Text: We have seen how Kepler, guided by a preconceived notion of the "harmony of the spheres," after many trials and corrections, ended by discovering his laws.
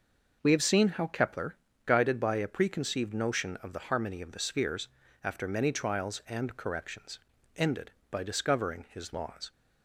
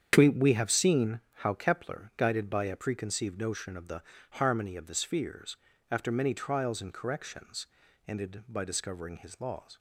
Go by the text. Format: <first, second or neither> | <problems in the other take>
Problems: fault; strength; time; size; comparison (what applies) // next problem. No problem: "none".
first | starts louder than the rest; strong; until 1.1 s; 8 dB // says "We" twice; at 0.2 s // pauses between "seen" and "how"; slight; at 1.2 s; 0.18 s long // pauses between "the" and "harmony"; slight; at 4.0 s; 0.30 s long